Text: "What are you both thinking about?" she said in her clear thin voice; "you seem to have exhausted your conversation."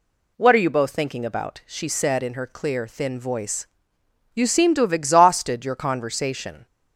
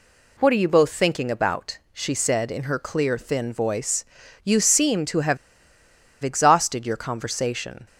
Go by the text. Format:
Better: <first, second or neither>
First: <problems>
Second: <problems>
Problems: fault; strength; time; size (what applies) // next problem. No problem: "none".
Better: first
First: none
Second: pauses between "have" and "exhausted"; noticeable; at 5.3 s; 0.86 s long